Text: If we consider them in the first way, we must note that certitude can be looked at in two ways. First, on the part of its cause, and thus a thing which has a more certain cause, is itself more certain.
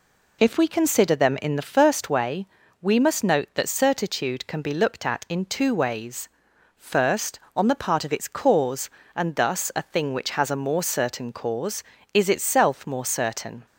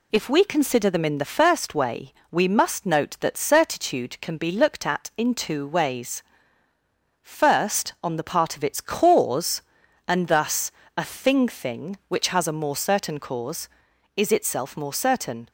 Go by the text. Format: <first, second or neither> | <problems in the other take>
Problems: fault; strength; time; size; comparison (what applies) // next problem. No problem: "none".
first | pauses between "thus" and "a"; slight; at 10.7 s; 0.24 s long // says "thing" twice; at 11.4 s